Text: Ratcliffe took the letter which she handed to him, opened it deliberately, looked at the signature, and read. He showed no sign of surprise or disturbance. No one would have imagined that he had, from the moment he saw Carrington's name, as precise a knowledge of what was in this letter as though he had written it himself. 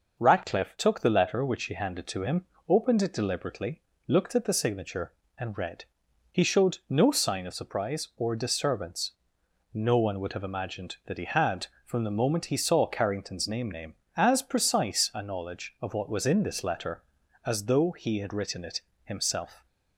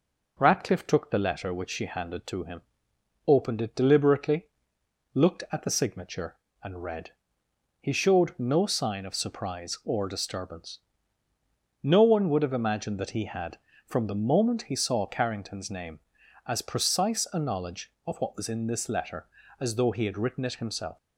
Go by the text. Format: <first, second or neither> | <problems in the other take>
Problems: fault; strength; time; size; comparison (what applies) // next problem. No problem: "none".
second | says "name" twice; at 13.6 s // pauses between "it" and "himself"; slight; at 18.8 s; 0.22 s long